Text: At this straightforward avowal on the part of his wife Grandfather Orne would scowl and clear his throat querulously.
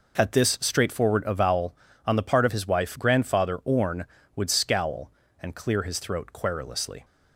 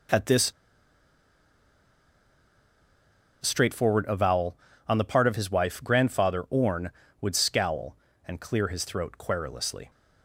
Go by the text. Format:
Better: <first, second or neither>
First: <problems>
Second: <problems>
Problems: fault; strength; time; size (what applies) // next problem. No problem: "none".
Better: first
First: none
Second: pauses between "this" and "straightforward"; strong; at 0.5 s; 2.9 s long